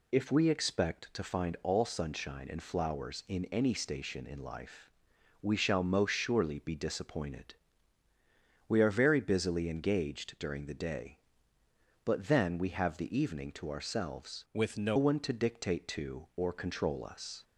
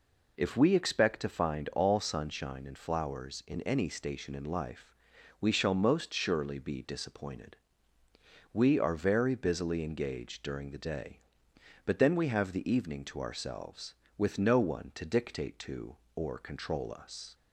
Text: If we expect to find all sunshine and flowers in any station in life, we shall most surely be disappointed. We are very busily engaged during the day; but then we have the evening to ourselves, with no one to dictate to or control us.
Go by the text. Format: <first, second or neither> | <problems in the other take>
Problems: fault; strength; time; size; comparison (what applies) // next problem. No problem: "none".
second | changes voice from "with" to "no"; from 14.5 to 14.9 s; 0.4 s long